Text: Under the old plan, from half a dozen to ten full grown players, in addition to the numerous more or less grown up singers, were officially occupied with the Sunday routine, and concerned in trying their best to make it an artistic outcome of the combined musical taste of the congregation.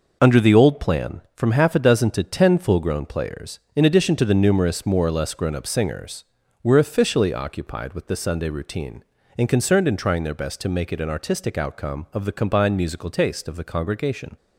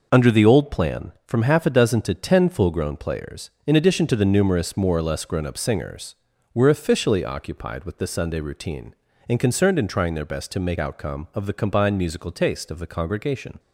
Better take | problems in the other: first | skips "it an artistic"; at 10.7 s

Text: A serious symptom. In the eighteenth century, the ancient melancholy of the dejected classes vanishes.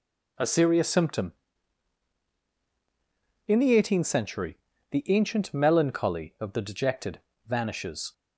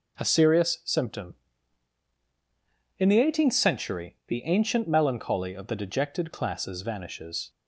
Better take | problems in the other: second | skips "classes"; at 7.3 s

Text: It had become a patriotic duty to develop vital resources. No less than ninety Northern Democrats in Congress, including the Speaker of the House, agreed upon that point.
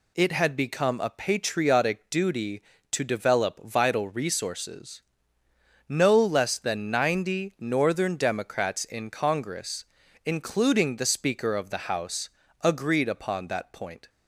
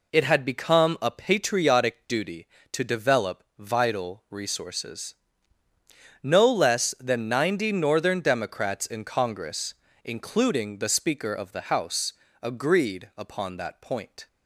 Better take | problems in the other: neither | none

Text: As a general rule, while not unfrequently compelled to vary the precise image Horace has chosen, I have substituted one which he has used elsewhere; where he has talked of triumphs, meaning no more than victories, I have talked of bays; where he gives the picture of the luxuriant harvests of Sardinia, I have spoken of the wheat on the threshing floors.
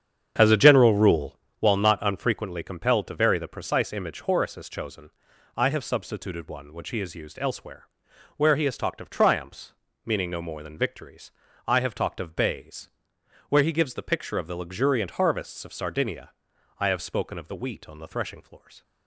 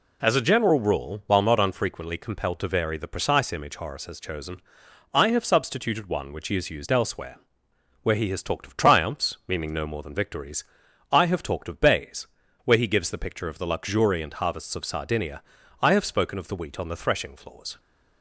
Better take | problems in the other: second | starts louder than the rest; strong; until 1.6 s; 8 dB

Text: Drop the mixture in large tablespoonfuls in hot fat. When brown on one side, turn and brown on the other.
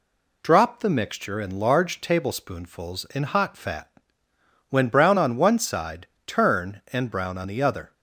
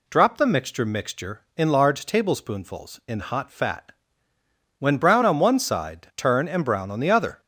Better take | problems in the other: first | says "mixture" twice; at 0.8 s

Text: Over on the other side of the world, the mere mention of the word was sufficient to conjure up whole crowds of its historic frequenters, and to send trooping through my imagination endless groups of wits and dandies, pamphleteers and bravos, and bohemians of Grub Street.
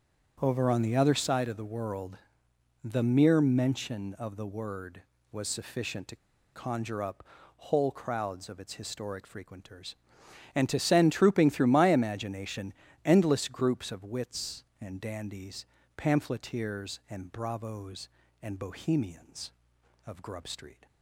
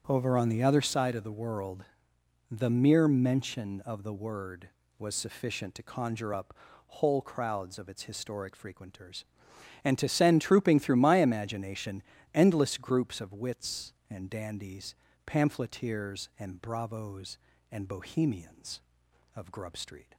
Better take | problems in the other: second | starts louder than the rest; strong; until 1.4 s; 7.5 dB; strong in the second // pauses between "to" and "conjure"; at 6.1 s; 0.38 s long // pauses between "up" and "whole"; slight; at 7.2 s; 0.34 s long; slight in the second // pauses between "imagination" and "endless"; slight; at 12.7 s; 0.32 s long; slight in the second

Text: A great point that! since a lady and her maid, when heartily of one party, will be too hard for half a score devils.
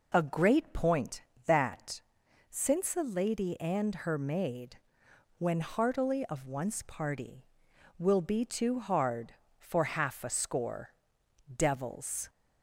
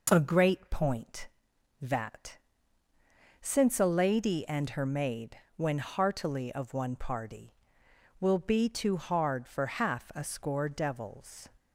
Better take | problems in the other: second | says "once" for "one"; at 6.4 s // pauses between "score" and "devils"; noticeable; at 10.8 s; 0.68 s long

